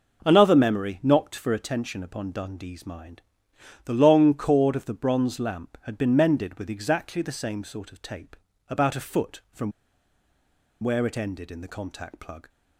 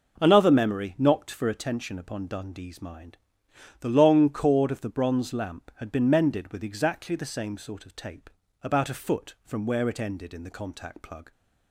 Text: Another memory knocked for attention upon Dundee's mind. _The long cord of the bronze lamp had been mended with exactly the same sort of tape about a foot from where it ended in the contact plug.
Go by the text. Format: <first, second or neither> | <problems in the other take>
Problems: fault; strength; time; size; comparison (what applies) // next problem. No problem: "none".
second | pauses between "tape" and "about"; slight; at 8.3 s; 0.34 s long; slight in the second // pauses between "from" and "where"; at 9.7 s; 1.1 s long